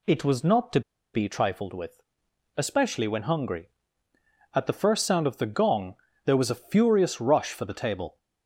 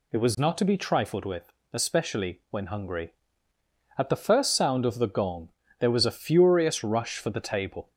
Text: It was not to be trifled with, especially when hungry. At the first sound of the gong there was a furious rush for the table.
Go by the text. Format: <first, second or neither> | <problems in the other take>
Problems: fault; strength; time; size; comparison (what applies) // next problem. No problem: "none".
second | pauses between "to" and "be"; slight; at 0.8 s; 0.33 s long // pauses between "gong" and "there"; slight; at 5.9 s; 0.30 s long; slight in the second